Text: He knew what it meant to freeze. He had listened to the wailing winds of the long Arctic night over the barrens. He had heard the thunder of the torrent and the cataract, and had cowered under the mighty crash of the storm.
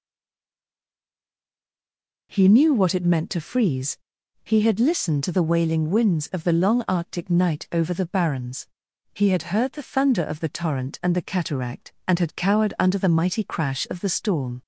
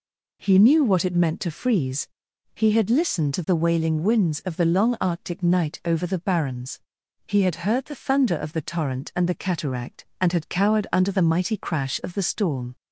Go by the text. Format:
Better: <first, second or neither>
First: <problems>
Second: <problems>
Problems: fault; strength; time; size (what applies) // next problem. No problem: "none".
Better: second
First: stays silent before the first word; until 2.3 s; 2.3 s long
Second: none